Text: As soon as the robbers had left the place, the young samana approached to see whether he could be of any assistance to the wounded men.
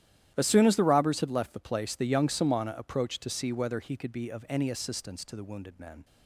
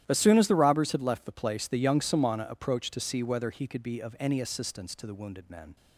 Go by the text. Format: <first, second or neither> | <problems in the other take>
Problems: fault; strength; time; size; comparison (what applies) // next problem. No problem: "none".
neither | starts louder than the rest; strong; the same in both